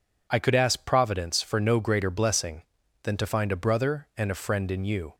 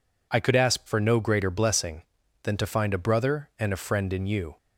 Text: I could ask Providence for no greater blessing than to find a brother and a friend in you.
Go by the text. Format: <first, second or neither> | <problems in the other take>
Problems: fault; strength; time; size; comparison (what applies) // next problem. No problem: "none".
first | skips "Providence"; at 0.8 s